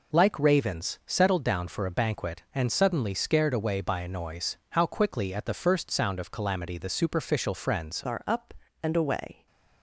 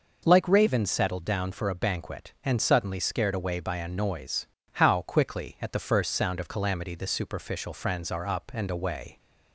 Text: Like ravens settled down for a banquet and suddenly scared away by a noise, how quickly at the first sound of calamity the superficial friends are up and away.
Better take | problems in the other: second | changes voice at "are"; from 8.0 s on; 1.4 s long

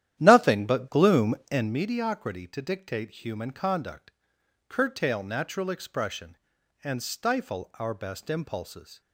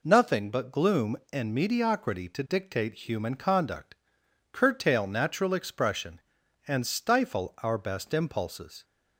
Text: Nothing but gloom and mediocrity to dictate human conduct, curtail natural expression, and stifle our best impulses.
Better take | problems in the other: second | starts louder than the rest; strong; until 1.8 s; 11.5 dB

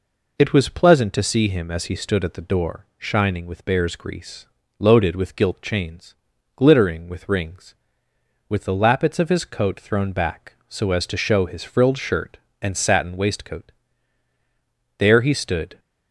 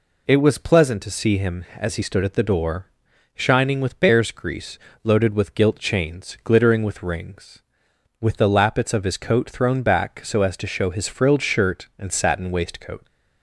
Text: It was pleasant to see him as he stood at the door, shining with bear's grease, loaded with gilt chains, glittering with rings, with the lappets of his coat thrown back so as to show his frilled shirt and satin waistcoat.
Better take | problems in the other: second | goes on to say "There he stood"; noticeable; from 14.9 s on; 0.80 s long

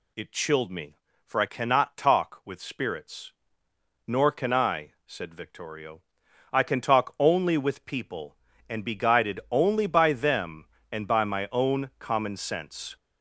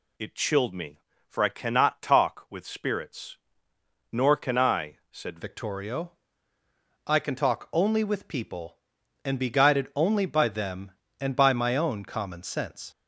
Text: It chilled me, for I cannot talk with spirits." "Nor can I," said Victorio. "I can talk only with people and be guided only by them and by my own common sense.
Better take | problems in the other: first | changes voice at "Victorio"; from 5.4 s on; 7.4 s long

